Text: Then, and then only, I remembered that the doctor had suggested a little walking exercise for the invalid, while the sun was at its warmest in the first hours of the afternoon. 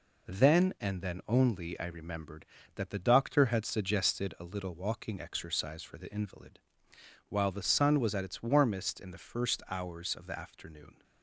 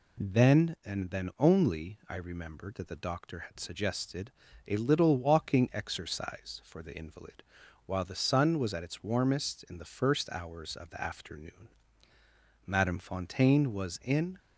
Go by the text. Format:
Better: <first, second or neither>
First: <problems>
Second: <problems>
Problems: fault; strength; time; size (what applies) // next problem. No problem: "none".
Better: first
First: none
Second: pauses between "suggested" and "a"; slight; at 4.3 s; 0.34 s long // goes on to say "Madame Fontaine was in"; strong; from 12.6 s on; 1.7 s long